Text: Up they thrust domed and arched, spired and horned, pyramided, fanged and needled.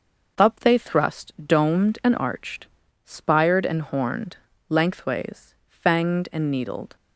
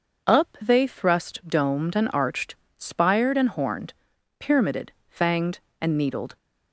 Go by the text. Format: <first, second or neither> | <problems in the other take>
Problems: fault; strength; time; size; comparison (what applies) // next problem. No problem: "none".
second | says "lengthways" for "pyramided"; at 4.6 s